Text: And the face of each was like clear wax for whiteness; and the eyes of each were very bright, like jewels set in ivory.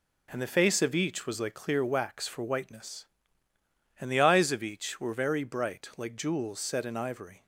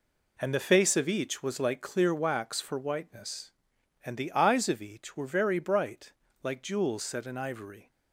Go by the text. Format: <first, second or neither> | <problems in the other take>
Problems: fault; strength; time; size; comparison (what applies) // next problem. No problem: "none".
neither | none